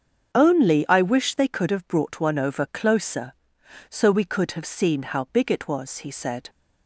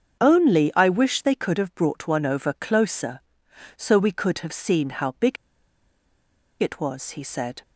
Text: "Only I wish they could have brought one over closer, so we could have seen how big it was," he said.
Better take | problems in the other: first | starts louder than the rest; until 1.2 s; 7 dB; also in the first // pauses between "big" and "it"; strong; at 5.3 s; 1.2 s long

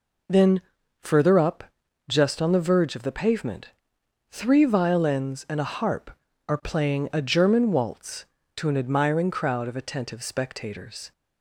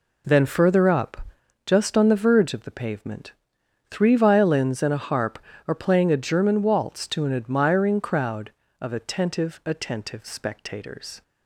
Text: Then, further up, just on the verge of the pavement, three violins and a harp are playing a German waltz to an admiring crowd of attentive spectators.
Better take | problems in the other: first | says "attentive" twice; at 9.6 s

